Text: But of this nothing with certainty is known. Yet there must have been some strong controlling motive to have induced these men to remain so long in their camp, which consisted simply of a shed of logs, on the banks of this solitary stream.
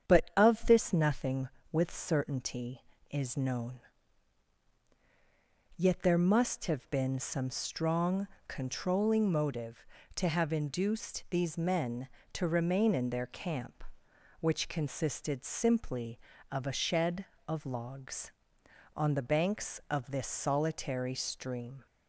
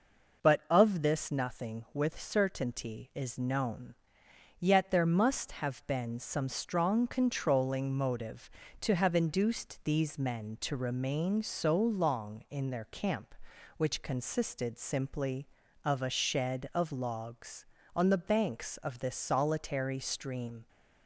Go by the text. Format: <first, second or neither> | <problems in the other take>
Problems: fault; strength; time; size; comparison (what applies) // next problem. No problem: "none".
second | starts louder than the rest; strong; until 1.1 s; 8 dB // pauses between "strong" and "controlling"; slight; at 8.2 s; 0.18 s long // skips "so long"; at 12.9 s